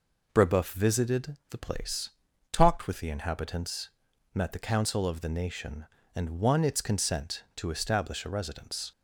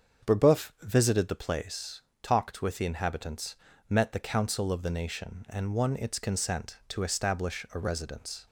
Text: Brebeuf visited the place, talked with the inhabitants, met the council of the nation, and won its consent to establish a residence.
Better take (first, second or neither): first